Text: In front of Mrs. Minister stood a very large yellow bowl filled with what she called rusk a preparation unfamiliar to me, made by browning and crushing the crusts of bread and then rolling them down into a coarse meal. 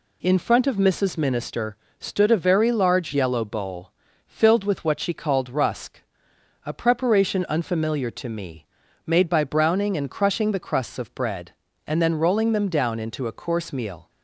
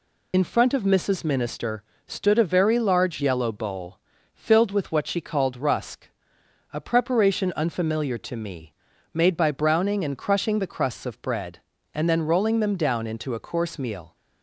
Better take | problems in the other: first | loses the start of "In"; at 0.3 s; 75 ms // pauses between "Minister" and "stood"; slight; at 1.8 s; 0.24 s long; slight in the first // pauses between "bowl" and "filled"; slight; at 3.9 s; 0.36 s long; slight in the first // pauses between "rusk" and "a"; noticeable; at 6.0 s; 0.64 s long; noticeable in the first

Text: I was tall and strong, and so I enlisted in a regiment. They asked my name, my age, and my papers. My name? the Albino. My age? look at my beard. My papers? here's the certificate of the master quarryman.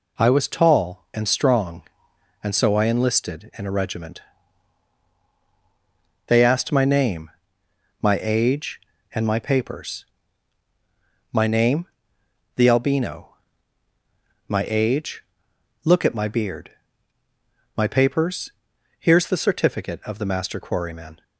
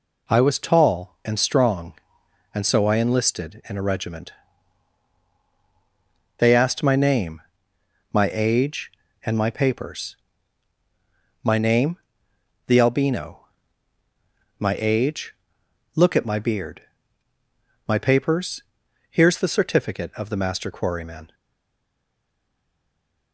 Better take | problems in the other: first | stays silent after the last word; noticeable; from 21.3 s on; 2.0 s long

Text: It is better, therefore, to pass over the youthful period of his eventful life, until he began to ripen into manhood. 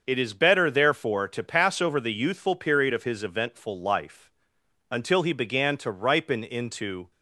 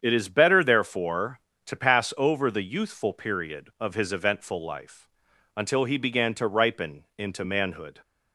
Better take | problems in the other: second | starts louder than the rest; until 1.0 s; 6.5 dB; strong in the second // stops before "manhood"; at 7.1 s

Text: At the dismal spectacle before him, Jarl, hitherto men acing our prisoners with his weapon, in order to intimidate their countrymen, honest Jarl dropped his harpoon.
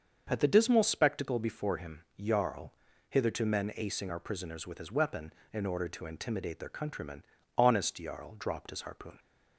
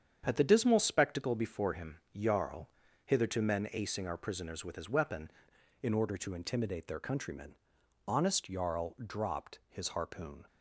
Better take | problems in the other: first | starts louder than the rest; strong; until 1.2 s; 8 dB; also in the first // changes voice at "in"; from 5.8 s on; 4.6 s long

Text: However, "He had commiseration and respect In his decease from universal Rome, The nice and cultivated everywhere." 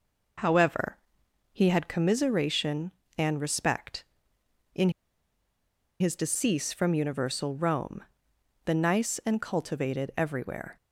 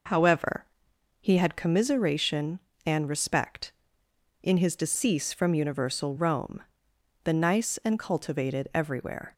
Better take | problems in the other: second | pauses between "In" and "his"; at 4.9 s; 1.0 s long

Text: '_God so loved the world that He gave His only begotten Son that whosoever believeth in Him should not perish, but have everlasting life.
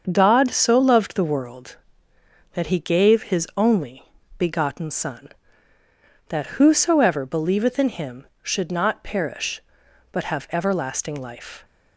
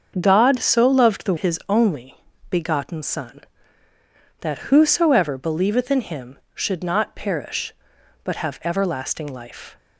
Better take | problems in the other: first | starts louder than the rest; until 1.2 s; 6.5 dB; also in the first // skips "world that He gave"; at 1.3 s // pauses between "only" and "begotten"; slight; at 2.1 s; 0.32 s long; slight in the first

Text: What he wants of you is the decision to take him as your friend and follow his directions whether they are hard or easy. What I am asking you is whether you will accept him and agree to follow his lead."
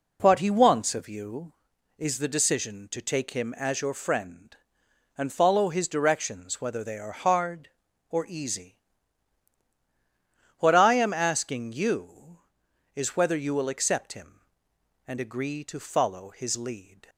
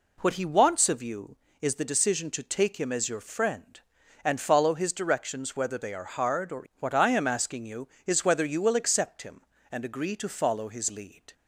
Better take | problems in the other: first | skips "easy"; at 6.7 s

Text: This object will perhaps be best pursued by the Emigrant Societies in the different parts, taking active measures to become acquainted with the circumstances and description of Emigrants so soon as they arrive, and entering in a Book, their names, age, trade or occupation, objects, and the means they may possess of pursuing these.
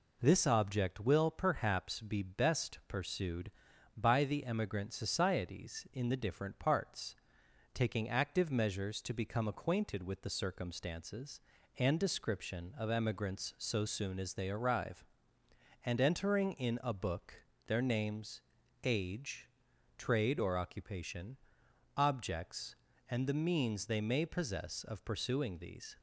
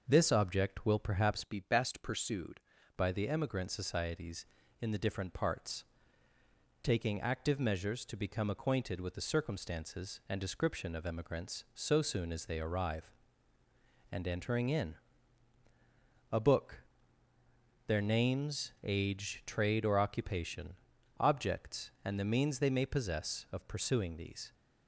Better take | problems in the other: first | starts louder than the rest; noticeable; until 1.0 s; 6 dB // changes voice from "be" to "pursued"; from 1.4 to 2.6 s; 1.2 s long // pauses between "in" and "a"; strong; at 14.9 s; 1.3 s long

